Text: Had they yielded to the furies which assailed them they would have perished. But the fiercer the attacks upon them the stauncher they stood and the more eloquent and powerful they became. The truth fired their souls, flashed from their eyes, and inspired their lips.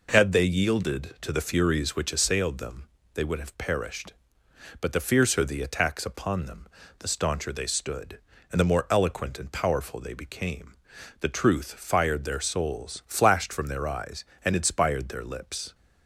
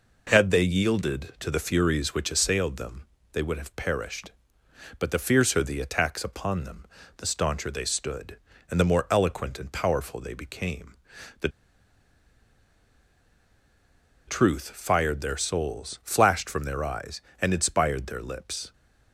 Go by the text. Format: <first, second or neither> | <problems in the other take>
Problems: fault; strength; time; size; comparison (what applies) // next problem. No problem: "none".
first | pauses between "them" and "they"; slight; at 3.0 s; 0.26 s long; slight in the first // pauses between "them" and "the"; slight; at 6.8 s; 0.32 s long; slight in the first // pauses between "The" and "truth"; strong; at 11.4 s; 2.7 s long